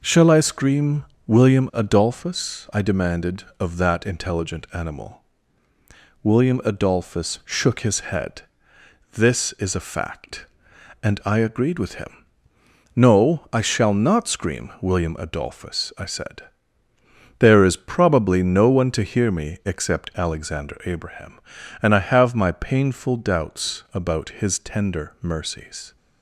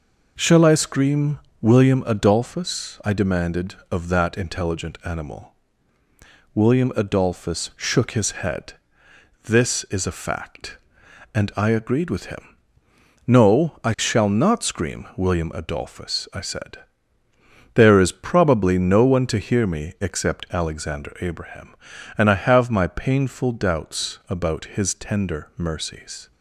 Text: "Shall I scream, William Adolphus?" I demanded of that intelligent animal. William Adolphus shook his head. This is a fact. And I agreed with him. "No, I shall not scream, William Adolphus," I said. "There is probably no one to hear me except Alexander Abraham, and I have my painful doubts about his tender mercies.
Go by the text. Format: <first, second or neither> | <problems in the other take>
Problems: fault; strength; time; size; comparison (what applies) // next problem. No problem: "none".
neither | none